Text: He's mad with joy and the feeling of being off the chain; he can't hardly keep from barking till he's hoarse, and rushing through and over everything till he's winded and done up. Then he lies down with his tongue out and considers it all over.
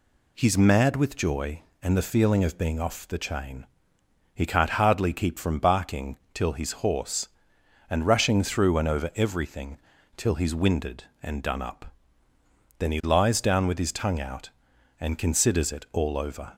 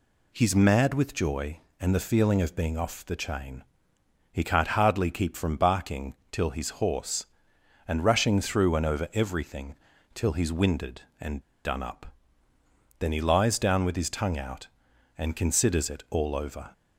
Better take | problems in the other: first | pauses between "barking" and "till"; slight; at 6.1 s; 0.16 s long; slight in the first // pauses between "everything" and "till"; at 9.7 s; 0.40 s long; also in the first // pauses between "and" and "done"; slight; at 11.3 s; 0.25 s long

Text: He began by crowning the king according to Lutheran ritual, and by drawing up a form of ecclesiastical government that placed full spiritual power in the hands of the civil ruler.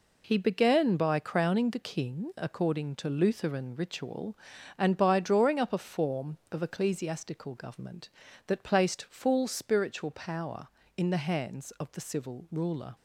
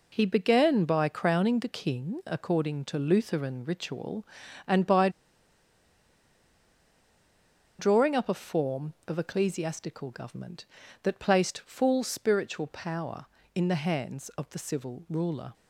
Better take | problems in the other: first | pauses between "by" and "drawing"; strong; at 5.0 s; 2.6 s long

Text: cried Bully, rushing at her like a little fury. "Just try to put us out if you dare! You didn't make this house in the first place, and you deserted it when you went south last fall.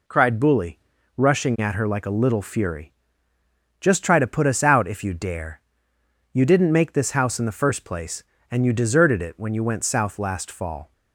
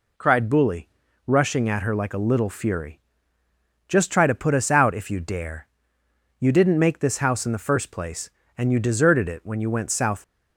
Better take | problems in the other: first | stops before "last fall"; at 10.2 s

